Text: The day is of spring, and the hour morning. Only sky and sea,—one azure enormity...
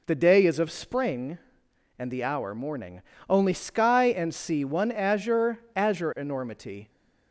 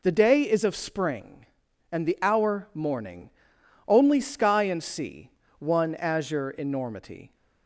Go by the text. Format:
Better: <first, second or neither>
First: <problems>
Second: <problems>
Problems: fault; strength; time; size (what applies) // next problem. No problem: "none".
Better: second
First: says "azure" twice; at 5.7 s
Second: none